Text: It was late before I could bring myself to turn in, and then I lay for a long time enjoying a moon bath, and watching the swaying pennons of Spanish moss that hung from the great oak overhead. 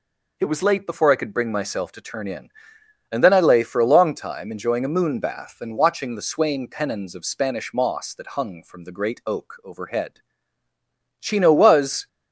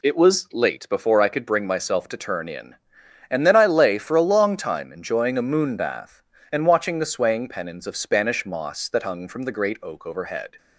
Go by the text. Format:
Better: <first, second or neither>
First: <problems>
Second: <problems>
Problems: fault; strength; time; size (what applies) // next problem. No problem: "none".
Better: second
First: goes on to say "Chino was"; noticeable; from 11.1 s on; 0.88 s long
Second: none